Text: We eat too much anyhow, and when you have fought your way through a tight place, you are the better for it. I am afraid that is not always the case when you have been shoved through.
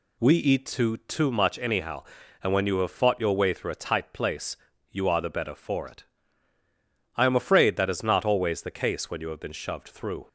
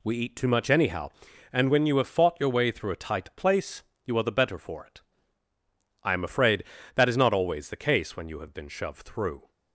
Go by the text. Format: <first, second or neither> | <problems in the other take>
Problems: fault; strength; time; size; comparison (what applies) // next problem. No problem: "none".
second | says "too" twice; at 0.9 s